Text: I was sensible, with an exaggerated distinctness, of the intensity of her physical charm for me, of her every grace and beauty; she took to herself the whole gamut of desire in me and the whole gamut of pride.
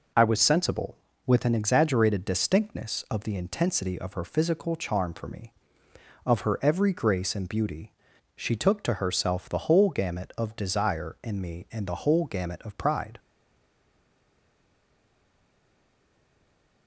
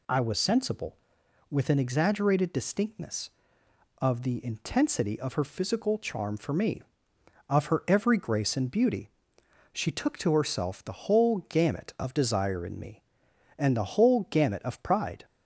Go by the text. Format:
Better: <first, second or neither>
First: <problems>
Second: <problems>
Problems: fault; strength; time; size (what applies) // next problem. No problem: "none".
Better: second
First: stays silent after the last word; strong; from 13.1 s on; 3.7 s long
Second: none